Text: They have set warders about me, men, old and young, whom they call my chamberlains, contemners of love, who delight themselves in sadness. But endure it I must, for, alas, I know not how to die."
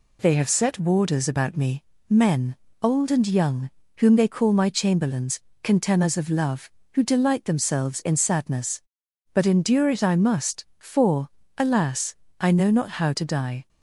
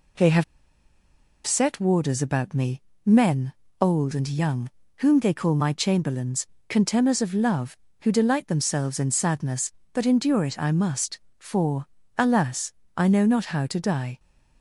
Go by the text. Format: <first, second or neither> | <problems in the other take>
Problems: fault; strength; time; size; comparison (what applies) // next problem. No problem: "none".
first | pauses between "have" and "set"; at 0.4 s; 1.0 s long